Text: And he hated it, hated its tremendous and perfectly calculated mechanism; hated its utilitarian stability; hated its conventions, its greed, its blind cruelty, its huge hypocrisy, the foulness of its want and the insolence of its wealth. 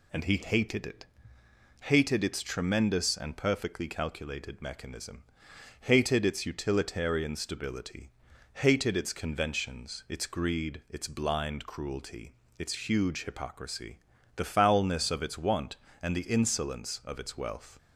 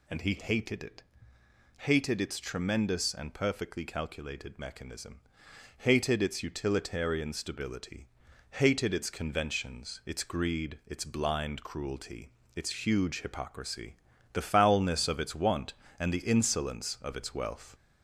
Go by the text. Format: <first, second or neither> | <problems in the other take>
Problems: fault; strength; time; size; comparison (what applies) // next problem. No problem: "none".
first | gets louder; slight; throughout; 3 dB